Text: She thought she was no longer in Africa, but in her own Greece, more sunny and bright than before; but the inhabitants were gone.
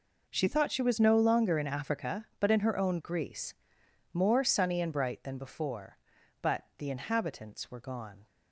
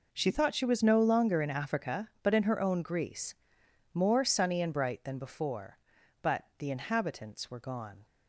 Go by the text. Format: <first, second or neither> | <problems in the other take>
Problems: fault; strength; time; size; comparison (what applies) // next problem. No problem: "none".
neither | none